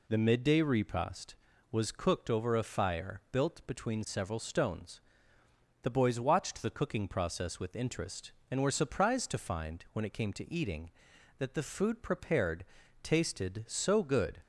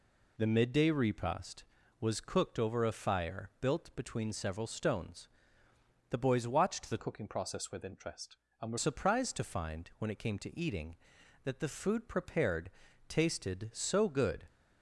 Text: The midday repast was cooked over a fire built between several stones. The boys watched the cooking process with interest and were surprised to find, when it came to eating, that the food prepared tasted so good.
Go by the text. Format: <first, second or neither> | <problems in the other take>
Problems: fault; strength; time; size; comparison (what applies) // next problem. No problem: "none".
first | changes voice from "cooking" to "were"; from 6.9 to 8.7 s; 1.8 s long // pauses between "prepared" and "tasted"; at 12.7 s; 0.38 s long; also in the first